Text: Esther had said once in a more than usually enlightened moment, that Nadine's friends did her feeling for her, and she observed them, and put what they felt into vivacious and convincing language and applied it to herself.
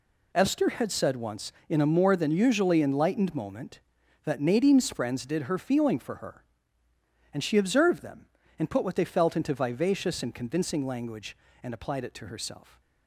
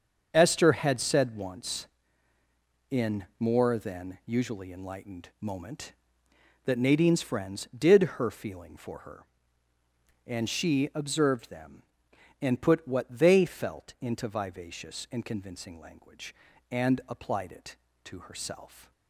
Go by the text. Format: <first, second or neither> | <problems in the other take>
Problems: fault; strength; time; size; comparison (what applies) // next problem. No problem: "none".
first | starts louder than the rest; until 1.3 s; 7 dB // skips "a"; at 3.3 s